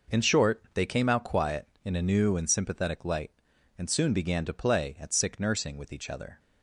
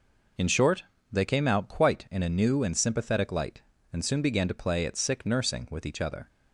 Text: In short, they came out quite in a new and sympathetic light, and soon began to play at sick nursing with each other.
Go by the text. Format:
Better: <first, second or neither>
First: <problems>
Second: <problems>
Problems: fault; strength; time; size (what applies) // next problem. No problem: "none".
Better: second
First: says "quiet" for "quite"; at 1.2 s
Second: none